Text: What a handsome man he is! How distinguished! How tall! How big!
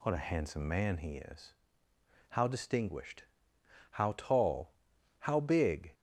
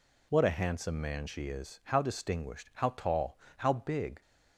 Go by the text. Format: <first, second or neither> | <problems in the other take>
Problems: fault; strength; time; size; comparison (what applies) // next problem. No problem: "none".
first | says "she" for "he"; at 1.2 s